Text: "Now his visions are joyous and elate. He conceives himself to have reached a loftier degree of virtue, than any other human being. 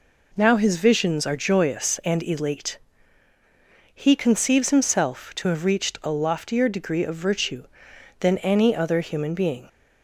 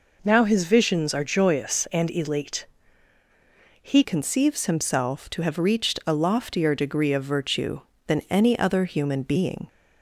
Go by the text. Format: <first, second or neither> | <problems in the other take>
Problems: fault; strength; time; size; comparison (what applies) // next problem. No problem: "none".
first | changes voice at "conceives"; from 4.0 s on; 5.6 s long